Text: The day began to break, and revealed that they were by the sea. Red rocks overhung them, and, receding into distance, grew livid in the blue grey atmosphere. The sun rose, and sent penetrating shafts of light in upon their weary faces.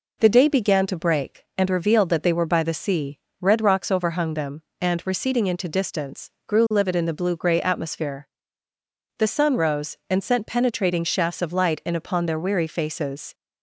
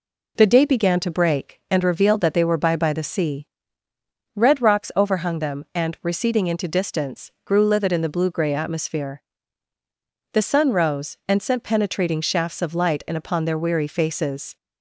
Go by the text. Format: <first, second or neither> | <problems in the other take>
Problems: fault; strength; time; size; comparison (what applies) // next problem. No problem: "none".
first | says "by" twice; at 2.7 s